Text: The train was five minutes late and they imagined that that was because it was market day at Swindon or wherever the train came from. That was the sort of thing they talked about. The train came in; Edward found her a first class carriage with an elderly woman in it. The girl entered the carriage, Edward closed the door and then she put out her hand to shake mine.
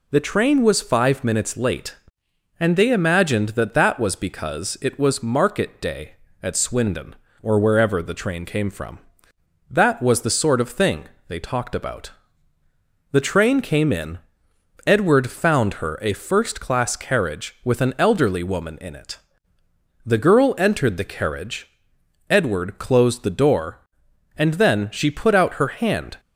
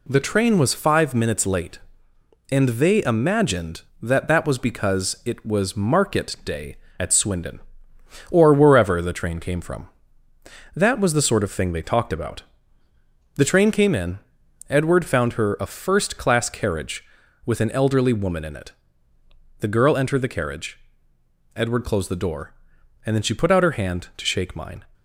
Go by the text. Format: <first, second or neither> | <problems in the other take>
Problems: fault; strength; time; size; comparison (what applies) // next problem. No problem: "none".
second | pauses between "thing" and "they"; slight; at 11.0 s; 0.24 s long // stops before "to shake mine"; at 26.1 s